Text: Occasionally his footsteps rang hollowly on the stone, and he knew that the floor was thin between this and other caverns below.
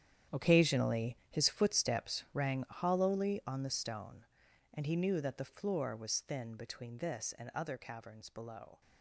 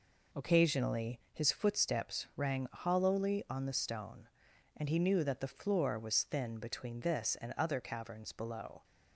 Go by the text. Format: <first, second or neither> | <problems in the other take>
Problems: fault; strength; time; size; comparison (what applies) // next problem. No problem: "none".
second | gets quieter; strong; throughout; 15 dB